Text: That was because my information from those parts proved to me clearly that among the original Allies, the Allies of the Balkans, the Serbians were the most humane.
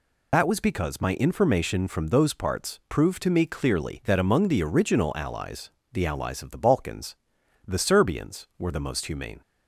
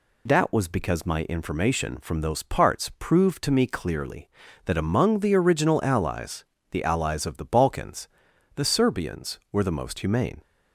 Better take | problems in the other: second | loses the start of "That"; at 0.3 s; 100 ms

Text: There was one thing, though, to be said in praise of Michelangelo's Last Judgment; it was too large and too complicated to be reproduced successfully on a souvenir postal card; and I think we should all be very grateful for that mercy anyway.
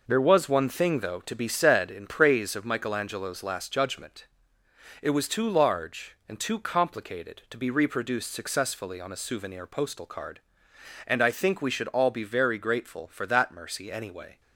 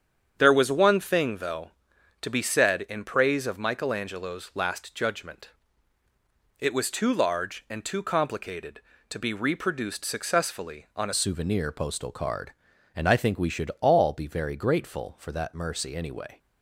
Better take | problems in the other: first | starts louder than the rest; strong; until 1.3 s; 8 dB // changes voice at "souvenir"; from 11.1 s on; 5.2 s long

